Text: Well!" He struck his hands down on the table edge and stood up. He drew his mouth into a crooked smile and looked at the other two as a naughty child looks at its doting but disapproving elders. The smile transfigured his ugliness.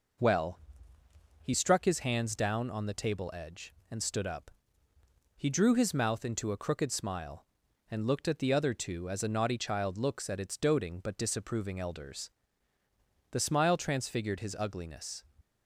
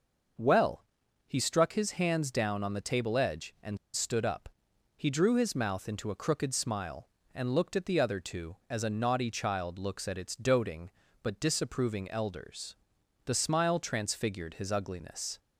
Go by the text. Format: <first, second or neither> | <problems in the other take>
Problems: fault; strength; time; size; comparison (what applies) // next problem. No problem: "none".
first | pauses between "and" and "stood"; slight; at 3.7 s; 0.17 s long